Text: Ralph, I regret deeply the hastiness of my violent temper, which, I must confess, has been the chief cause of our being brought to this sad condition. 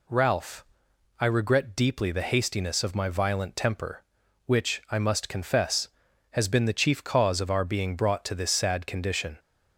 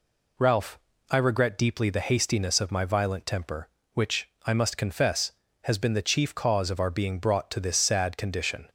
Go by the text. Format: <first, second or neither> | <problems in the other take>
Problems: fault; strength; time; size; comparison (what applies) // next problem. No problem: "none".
neither | none